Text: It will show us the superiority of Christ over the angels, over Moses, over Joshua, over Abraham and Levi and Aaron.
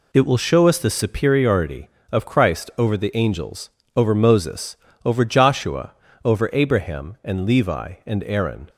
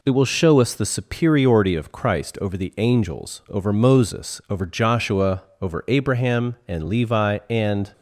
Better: first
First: none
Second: stops before "Aaron"; at 7.9 s

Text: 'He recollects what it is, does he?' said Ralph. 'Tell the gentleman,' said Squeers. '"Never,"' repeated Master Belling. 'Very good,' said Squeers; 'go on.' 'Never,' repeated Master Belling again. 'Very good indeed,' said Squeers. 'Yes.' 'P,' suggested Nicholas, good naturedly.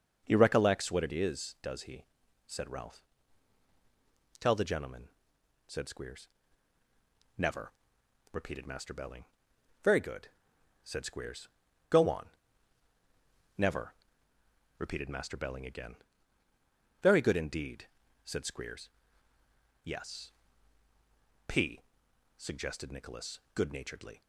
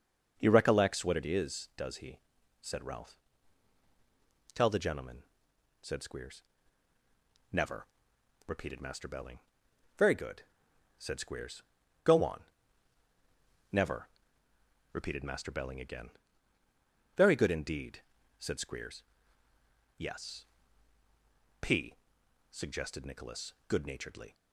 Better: neither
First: starts louder than the rest; until 1.2 s; 6.5 dB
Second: starts louder than the rest; until 1.3 s; 6.5 dB

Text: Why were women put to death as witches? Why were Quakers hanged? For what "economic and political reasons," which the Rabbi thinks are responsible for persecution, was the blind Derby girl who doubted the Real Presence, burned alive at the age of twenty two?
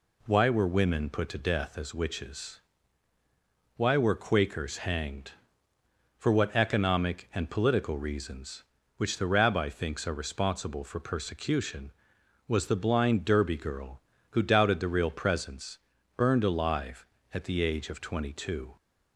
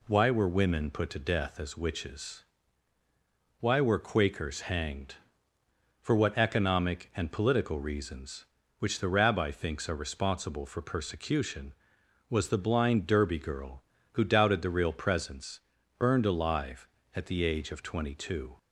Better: neither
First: none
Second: none

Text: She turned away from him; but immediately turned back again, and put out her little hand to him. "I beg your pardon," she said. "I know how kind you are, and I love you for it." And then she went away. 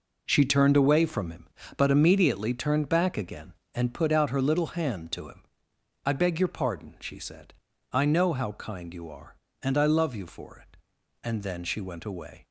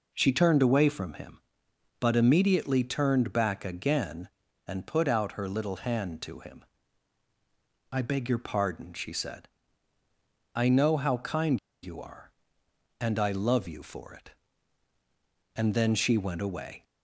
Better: first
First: none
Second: pauses between "kind" and "you"; slight; at 11.5 s; 0.24 s long

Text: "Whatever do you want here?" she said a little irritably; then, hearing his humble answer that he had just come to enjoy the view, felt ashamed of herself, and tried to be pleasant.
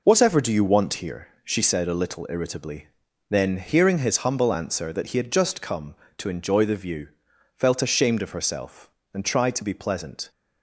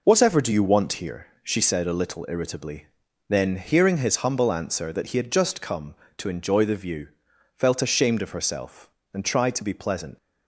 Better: first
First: none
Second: leaves "pleasant" unfinished; at 10.1 s; 115 ms

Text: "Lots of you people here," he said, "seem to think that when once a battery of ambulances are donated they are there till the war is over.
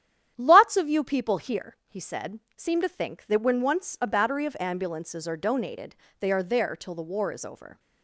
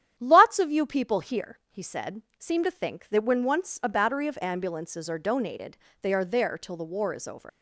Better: first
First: starts louder than the rest; strong; until 1.3 s; 10 dB // pauses between "donated" and "they"; slight; at 5.9 s; 0.24 s long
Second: starts louder than the rest; strong; until 1.1 s; 10 dB // pauses between "donated" and "they"; slight; at 5.7 s; 0.24 s long // leaves "over" unfinished; at 7.4 s; 125 ms

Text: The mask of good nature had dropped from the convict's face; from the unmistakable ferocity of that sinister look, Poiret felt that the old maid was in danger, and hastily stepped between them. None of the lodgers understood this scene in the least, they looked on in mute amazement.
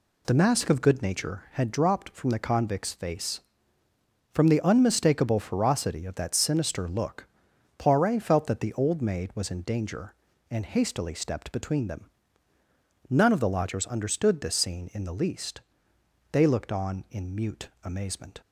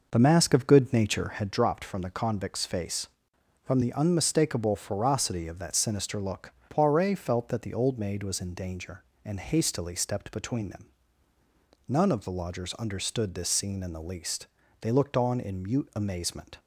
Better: first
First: none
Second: starts louder than the rest; noticeable; until 1.6 s; 5.5 dB

